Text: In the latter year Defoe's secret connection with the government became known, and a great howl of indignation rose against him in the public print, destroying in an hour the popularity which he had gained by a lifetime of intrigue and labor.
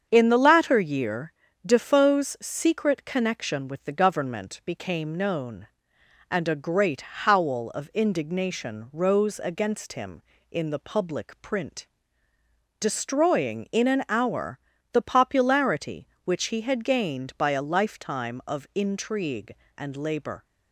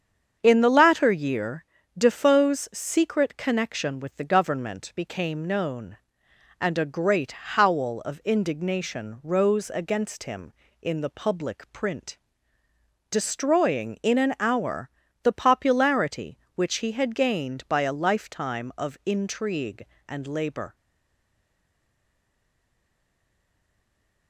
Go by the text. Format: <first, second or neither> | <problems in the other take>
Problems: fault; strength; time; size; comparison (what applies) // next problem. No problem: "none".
first | starts louder than the rest; strong; until 1.4 s; 7.5 dB; strong in the first // pauses between "year" and "Defoe's"; slight; at 1.6 s; 0.32 s long; slight in the first // pauses between "hour" and "the"; slight; at 14.9 s; 0.32 s long; slight in the first // stays silent after the last word; strong; from 20.7 s on; 3.5 s long